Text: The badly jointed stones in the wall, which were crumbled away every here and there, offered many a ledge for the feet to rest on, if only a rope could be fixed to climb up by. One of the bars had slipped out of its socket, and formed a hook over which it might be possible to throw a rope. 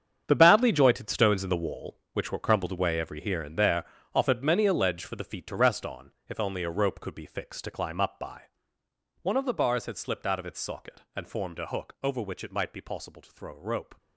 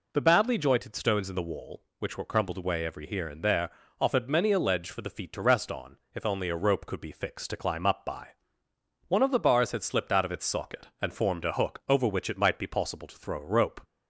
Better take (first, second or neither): second